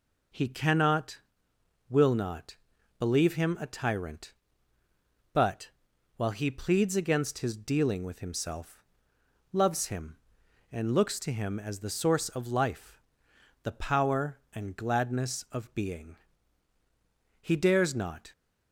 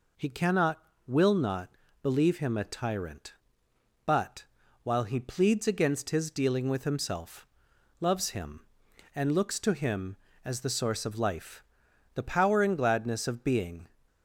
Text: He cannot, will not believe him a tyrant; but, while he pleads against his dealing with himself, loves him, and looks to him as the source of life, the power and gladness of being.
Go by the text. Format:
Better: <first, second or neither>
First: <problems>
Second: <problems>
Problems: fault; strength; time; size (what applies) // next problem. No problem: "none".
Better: second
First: pauses between "not" and "believe"; at 2.5 s; 0.42 s long // goes on to say "He dares not"; noticeable; from 17.4 s on; 0.90 s long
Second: pauses between "not" and "believe"; slight; at 1.6 s; 0.34 s long